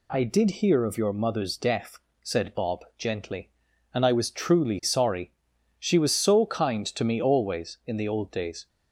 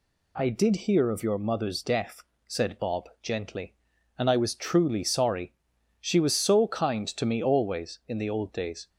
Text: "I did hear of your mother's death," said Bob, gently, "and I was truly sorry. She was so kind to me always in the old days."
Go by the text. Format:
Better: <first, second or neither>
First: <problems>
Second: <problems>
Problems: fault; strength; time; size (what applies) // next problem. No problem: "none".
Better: neither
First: none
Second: none